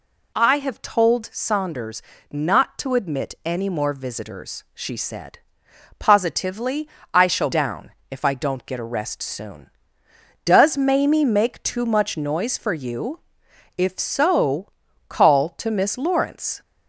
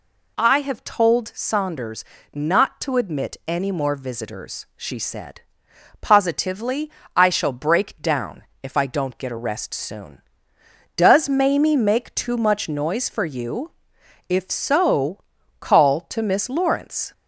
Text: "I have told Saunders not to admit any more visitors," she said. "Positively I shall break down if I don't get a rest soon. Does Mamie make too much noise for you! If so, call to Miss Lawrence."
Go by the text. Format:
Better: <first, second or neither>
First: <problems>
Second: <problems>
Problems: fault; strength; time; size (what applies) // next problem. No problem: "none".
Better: second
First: pauses between "Saunders" and "not"; slight; at 2.0 s; 0.30 s long // pauses between "Positively" and "I"; slight; at 6.8 s; 0.26 s long // skips "break"; at 7.5 s // pauses between "down" and "if"; slight; at 7.9 s; 0.18 s long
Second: pauses between "Saunders" and "not"; slight; at 2.0 s; 0.30 s long // pauses between "Positively" and "I"; slight; at 6.8 s; 0.26 s long // pauses between "down" and "if"; slight; at 8.4 s; 0.18 s long